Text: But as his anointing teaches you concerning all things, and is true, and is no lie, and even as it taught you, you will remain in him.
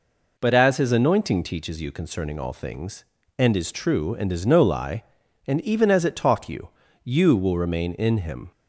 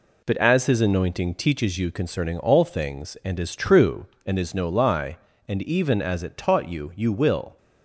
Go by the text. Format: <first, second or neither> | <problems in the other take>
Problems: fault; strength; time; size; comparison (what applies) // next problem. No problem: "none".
first | stops before "remain in him"; at 7.5 s